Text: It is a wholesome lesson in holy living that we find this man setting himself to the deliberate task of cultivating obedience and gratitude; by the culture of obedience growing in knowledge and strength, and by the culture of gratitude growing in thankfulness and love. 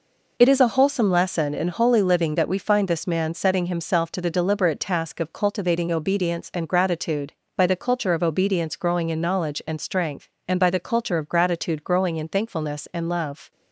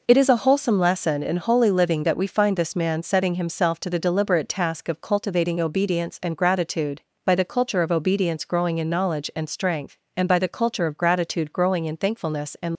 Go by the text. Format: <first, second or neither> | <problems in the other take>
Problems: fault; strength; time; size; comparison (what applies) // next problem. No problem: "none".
first | stops before "love"; at 12.7 s